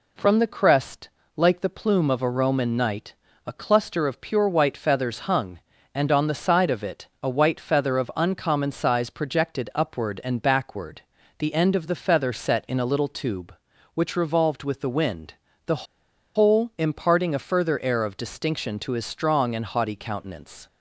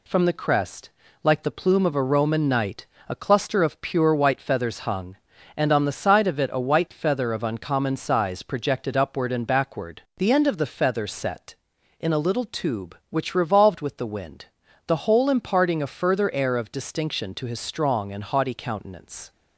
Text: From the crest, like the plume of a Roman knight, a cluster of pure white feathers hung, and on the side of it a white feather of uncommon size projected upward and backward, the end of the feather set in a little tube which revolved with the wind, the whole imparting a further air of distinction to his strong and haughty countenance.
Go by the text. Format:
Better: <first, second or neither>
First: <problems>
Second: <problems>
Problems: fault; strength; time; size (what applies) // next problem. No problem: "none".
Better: second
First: pauses between "it" and "a"; slight; at 7.0 s; 0.16 s long // pauses between "the" and "whole"; noticeable; at 15.8 s; 0.52 s long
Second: none